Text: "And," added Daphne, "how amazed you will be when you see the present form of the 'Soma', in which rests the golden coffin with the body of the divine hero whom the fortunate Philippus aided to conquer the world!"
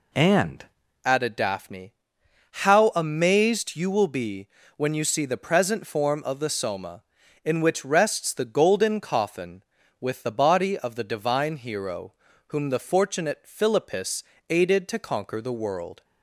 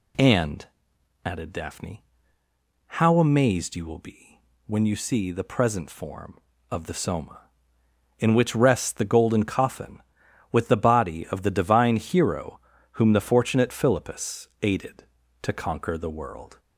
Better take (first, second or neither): second